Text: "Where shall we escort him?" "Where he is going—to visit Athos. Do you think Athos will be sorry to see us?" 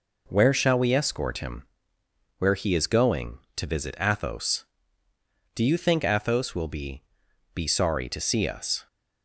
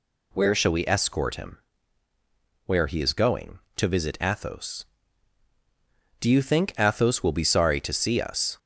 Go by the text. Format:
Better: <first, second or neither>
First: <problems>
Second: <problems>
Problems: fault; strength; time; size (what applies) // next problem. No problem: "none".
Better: second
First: says "be" twice; at 7.5 s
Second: none